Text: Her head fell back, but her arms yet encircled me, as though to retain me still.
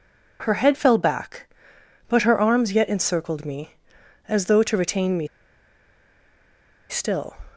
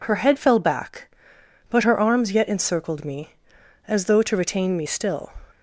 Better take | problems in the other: second | pauses between "me" and "still"; strong; at 5.2 s; 1.6 s long

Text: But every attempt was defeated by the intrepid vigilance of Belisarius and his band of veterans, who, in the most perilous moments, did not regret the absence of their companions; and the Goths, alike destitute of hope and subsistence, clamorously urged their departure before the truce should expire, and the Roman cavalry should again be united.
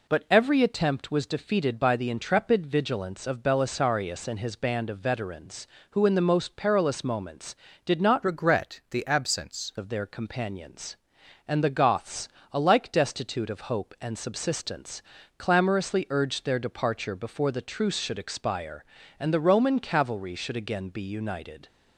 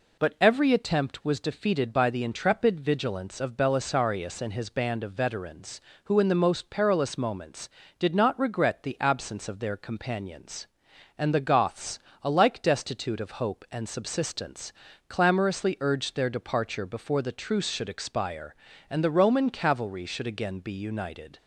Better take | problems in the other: second | changes voice from "regret" to "absence"; from 8.2 to 9.7 s; 1.5 s long

